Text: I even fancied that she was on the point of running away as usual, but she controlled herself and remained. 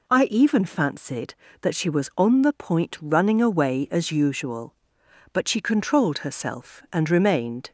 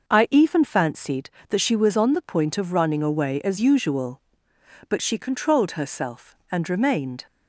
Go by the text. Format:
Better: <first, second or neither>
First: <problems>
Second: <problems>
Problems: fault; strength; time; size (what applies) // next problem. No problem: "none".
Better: second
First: skips "of"; at 2.9 s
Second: none